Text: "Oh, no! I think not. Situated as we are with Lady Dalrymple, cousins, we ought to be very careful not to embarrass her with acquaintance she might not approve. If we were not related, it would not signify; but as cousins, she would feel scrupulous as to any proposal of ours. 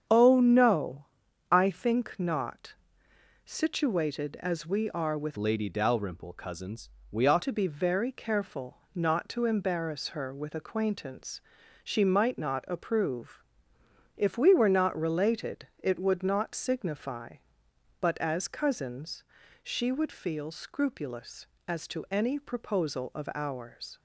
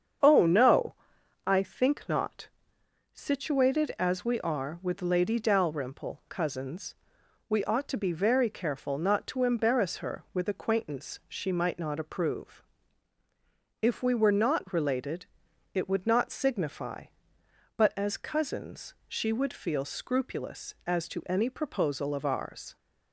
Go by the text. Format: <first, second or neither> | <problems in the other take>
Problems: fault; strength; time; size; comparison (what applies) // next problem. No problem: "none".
second | starts louder than the rest; strong; until 1.5 s; 8 dB; strong in the second // changes voice from "Lady" to "ought"; from 5.3 to 7.4 s; 2.1 s long // pauses between "careful" and "not"; slight; at 8.7 s; 0.18 s long // pauses between "acquaintance" and "she"; at 11.4 s; 0.42 s long